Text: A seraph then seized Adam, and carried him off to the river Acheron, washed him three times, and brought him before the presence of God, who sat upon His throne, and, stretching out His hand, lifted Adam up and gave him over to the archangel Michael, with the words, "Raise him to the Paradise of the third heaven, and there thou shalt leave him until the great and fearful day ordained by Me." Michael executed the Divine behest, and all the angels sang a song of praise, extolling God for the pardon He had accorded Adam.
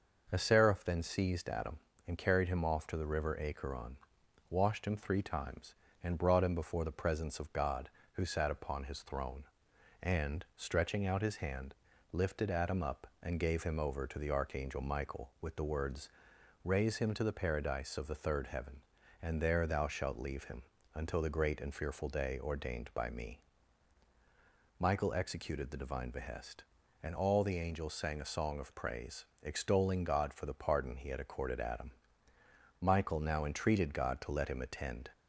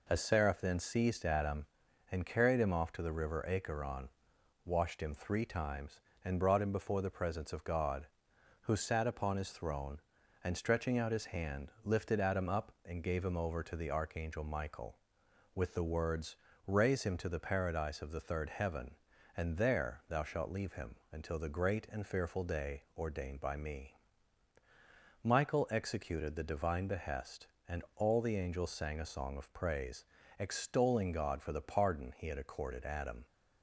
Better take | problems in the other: second | pauses between "him" and "until"; slight; at 20.6 s; 0.32 s long; slight in the second // goes on to say "Michael now entreated God to let him attend"; strong; from 32.8 s on; 2.3 s long

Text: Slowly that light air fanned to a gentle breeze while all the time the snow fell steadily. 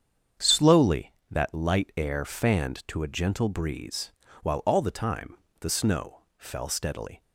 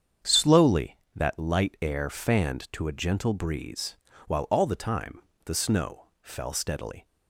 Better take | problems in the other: neither | starts louder than the rest; strong; the same in both // pauses between "breeze" and "while"; slight; the same in both // pauses between "time" and "the"; slight; the same in both // pauses between "snow" and "fell"; slight; the same in both

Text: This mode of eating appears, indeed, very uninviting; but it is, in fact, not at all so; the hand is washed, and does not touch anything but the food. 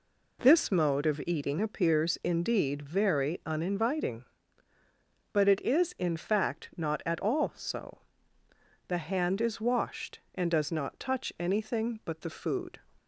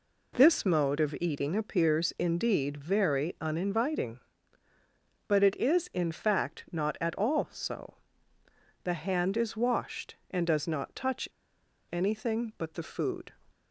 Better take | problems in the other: first | pauses between "touch" and "anything"; noticeable; at 11.2 s; 0.65 s long

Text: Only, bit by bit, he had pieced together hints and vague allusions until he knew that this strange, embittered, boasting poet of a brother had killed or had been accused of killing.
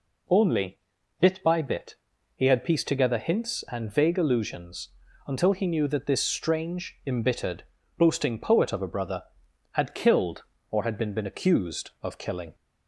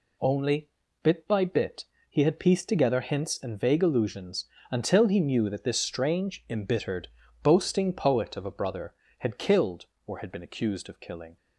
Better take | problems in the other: second | pauses between "allusions" and "until"; slight; at 4.8 s; 0.36 s long; slight in the second // says "been" twice; at 11.1 s

